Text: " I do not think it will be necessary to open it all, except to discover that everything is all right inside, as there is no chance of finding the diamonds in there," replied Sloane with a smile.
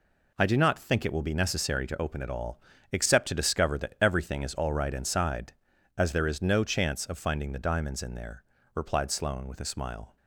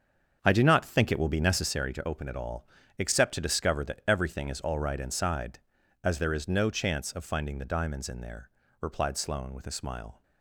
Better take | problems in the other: first | starts louder than the rest; until 1.7 s; 7 dB

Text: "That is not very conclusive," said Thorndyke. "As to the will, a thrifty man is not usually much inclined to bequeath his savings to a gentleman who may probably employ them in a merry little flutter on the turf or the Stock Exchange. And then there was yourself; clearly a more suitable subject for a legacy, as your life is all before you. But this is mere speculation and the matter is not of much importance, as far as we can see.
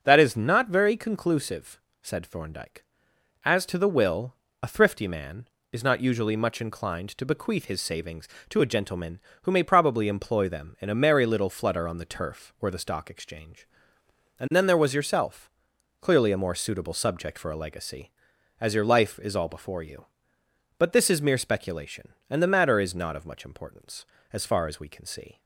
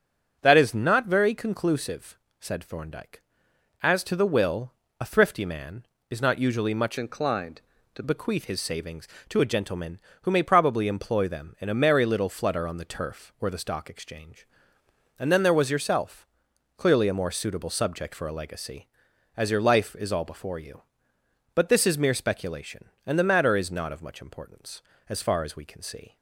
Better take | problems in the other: first | starts louder than the rest; until 1.4 s; 6.5 dB; also in the first // changes voice from "inclined" to "to"; from 6.9 to 8.0 s; 1.1 s long

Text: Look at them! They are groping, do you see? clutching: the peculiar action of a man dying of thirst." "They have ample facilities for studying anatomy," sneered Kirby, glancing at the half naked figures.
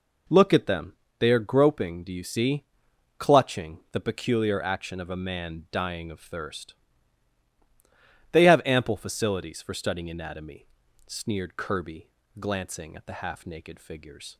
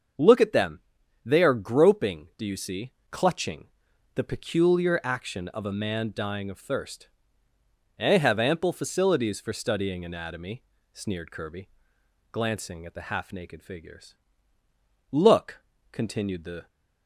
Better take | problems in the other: first | starts louder than the rest; until 1.6 s; 6.5 dB // goes on to say "Look continued the"; from 15.1 s on; 1.5 s long

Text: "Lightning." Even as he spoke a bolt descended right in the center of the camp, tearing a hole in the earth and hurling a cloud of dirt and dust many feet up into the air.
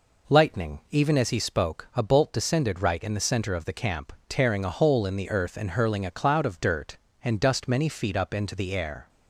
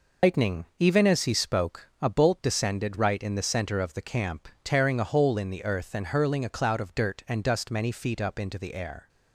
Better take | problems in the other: first | loses the start of "Lightning"; at 0.2 s; 135 ms

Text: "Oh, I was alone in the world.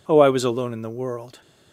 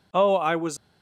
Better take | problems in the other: first | stops before "alone in the world"; at 0.7 s

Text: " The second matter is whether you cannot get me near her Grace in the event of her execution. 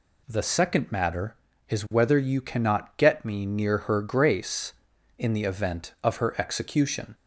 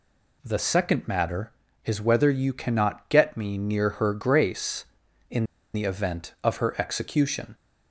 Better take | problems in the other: first | pauses between "in" and "the"; slight; at 5.4 s; 0.29 s long

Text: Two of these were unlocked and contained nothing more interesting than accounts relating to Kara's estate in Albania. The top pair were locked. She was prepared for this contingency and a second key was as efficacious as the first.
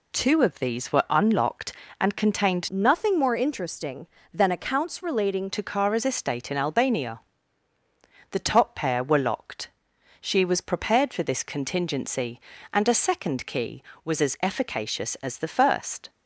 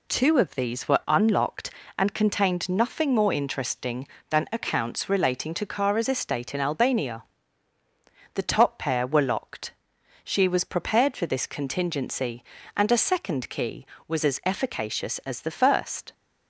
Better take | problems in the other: second | changes voice from "nothing" to "relating"; from 2.6 to 5.5 s; 2.9 s long

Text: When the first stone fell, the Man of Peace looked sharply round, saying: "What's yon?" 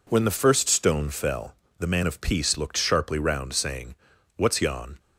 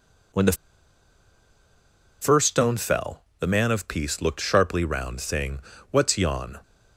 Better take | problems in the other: first | pauses between "the" and "first"; strong; at 0.5 s; 1.6 s long

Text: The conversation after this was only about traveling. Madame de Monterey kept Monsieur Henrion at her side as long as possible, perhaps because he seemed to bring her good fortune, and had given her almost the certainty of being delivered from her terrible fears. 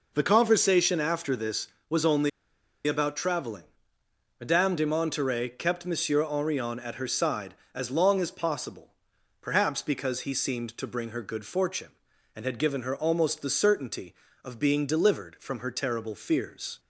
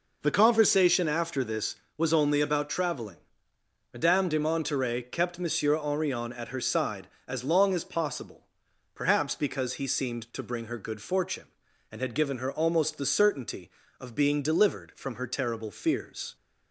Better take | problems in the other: second | pauses between "only" and "about"; noticeable; at 2.2 s; 0.57 s long

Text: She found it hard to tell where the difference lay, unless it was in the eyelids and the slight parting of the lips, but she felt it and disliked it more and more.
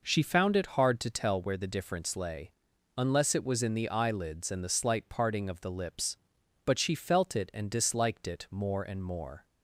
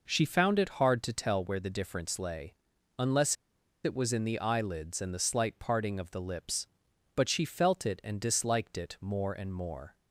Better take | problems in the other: first | pauses between "unless" and "it"; noticeable; at 3.3 s; 0.49 s long

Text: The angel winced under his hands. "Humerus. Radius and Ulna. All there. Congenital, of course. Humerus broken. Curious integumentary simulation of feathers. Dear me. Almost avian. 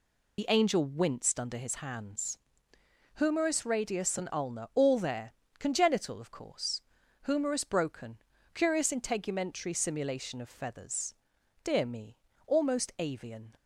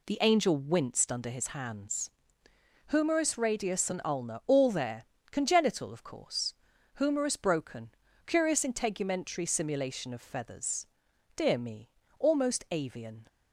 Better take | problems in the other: second | loses the start of "The"; at 0.3 s; 50 ms

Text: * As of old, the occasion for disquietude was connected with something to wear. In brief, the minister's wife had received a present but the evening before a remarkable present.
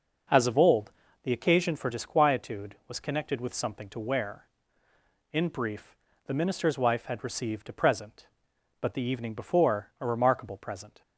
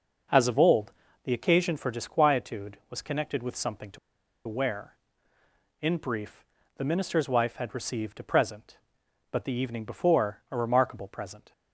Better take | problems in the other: first | pauses between "to" and "wear"; noticeable; at 3.9 s; 0.49 s long

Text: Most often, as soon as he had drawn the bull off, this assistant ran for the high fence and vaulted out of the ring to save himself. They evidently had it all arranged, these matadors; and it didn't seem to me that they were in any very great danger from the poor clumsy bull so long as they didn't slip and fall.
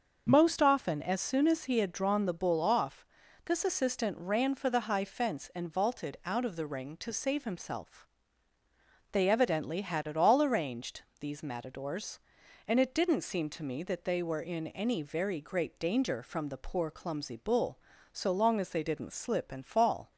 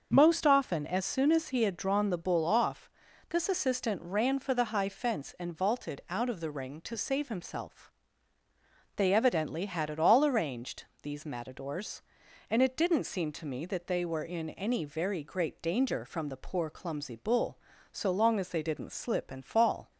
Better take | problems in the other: neither | starts louder than the rest; the same in both

